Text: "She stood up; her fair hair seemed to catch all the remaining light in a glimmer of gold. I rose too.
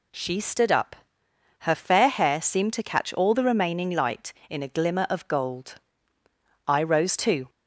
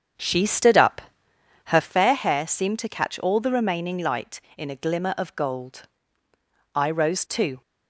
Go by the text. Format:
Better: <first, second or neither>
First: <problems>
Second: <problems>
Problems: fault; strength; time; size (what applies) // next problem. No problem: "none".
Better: first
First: none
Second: starts louder than the rest; strong; until 2.0 s; 7.5 dB